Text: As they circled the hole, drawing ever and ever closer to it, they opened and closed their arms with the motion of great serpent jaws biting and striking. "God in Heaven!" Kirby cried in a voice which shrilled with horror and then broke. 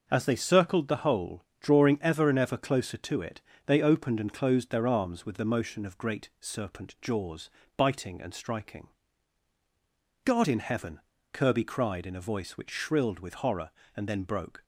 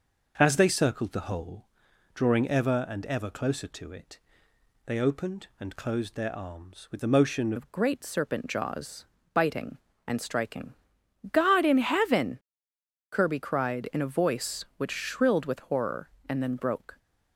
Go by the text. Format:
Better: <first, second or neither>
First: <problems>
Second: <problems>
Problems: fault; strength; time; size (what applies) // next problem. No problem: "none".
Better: first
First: pauses between "jaws" and "biting"; slight; at 7.4 s; 0.28 s long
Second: changes voice at "of"; from 7.5 s on; 9.4 s long // pauses between "jaws" and "biting"; slight; at 9.0 s; 0.28 s long